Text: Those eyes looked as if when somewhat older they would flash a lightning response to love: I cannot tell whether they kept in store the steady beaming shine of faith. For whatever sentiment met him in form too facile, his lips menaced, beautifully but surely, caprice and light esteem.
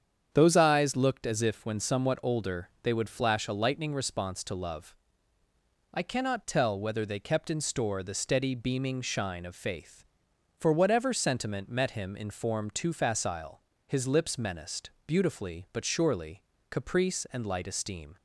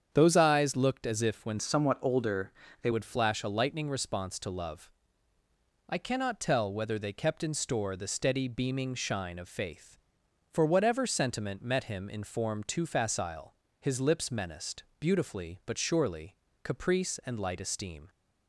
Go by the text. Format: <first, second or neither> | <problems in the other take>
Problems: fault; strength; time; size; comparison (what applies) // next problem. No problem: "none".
first | starts louder than the rest; strong; until 1.1 s; 8 dB; strong in the first // changes voice from "somewhat" to "they"; from 1.5 to 2.8 s; 1.3 s long // pauses between "older" and "they"; slight; at 2.5 s; 0.30 s long